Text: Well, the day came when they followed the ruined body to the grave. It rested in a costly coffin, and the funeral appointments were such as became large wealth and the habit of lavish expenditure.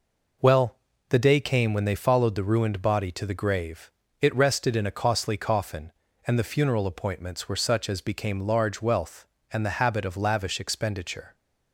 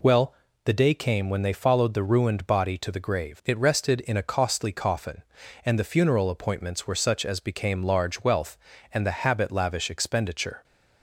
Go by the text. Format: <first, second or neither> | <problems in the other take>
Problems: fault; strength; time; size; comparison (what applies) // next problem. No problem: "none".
first | skips "of"; at 9.5 s